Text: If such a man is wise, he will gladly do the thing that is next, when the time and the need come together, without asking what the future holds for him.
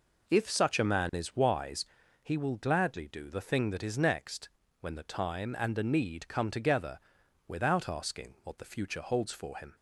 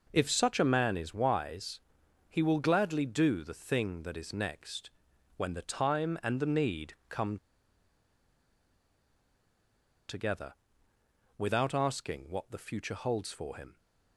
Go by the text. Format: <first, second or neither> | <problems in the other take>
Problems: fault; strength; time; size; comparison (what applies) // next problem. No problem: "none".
first | pauses between "need" and "come"; slight; at 6.9 s; 0.16 s long // pauses between "come" and "together"; strong; at 7.3 s; 2.7 s long